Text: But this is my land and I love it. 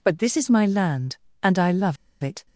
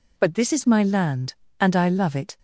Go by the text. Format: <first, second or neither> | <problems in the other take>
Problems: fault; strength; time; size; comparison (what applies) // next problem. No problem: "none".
second | pauses between "love" and "it"; slight; at 1.9 s; 0.27 s long